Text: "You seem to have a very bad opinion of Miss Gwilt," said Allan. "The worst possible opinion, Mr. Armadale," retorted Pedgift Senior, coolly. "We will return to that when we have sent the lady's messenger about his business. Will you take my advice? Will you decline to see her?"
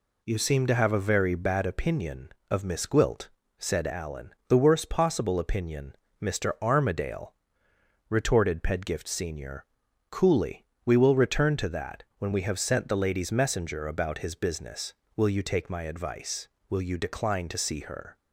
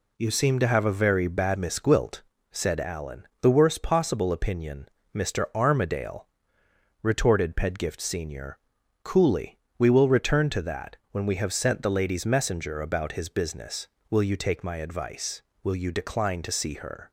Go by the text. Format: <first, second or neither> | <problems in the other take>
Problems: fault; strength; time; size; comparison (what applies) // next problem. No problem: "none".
first | skips "opinion of"; at 1.5 s // pauses between "that" and "when"; slight; at 10.9 s; 0.16 s long; slight in the first